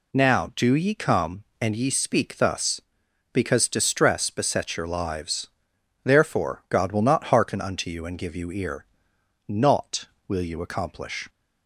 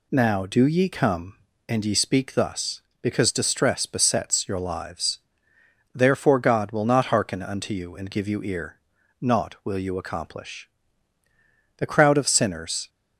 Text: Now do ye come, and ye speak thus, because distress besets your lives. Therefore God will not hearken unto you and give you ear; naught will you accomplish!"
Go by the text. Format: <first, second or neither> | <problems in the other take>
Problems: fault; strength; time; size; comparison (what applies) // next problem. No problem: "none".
first | goes on to say "The crowd of sinners"; noticeable; from 11.7 s on; 1.1 s long